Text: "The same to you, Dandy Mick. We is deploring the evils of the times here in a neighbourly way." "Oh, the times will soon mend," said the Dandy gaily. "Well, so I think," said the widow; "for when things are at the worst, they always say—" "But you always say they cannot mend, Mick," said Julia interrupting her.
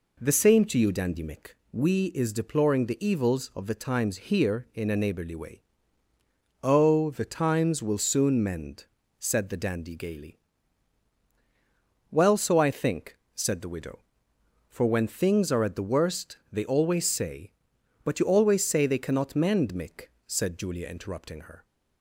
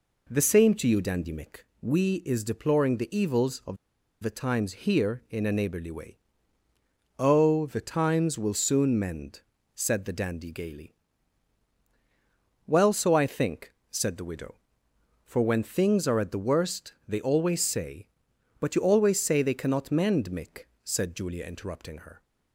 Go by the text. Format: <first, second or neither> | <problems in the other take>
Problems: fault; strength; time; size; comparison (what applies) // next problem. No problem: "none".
first | pauses between "of" and "the"; at 3.7 s; 0.44 s long